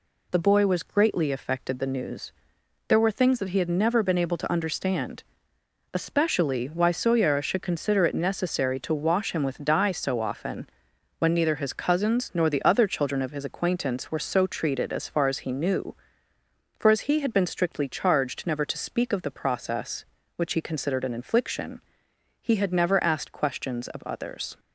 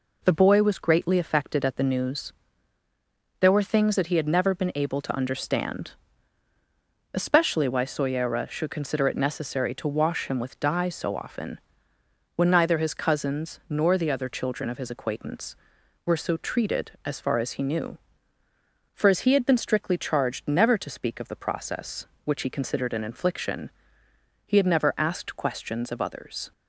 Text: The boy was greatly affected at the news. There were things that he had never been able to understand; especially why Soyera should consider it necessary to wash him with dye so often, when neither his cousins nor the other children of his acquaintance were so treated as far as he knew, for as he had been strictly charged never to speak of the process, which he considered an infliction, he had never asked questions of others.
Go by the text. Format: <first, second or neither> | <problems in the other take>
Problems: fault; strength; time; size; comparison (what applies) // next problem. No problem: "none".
second | skips "at"; at 1.7 s